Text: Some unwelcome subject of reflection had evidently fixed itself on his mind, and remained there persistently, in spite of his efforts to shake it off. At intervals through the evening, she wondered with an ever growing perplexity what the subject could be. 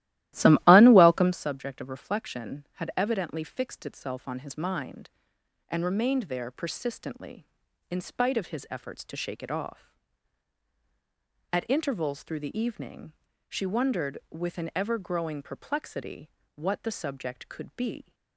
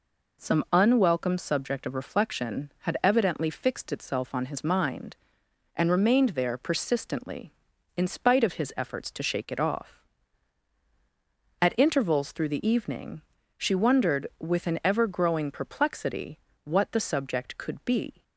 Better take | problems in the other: second | starts louder than the rest; strong; until 1.5 s; 15 dB // pauses between "perplexity" and "what"; slight; at 16.3 s; 0.26 s long; slight in the second

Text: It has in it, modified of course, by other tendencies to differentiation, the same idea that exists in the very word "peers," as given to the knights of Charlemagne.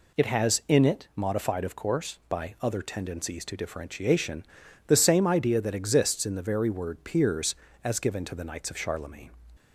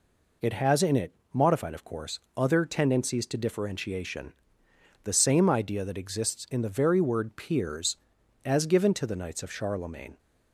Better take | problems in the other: first | skips "by"; at 2.2 s

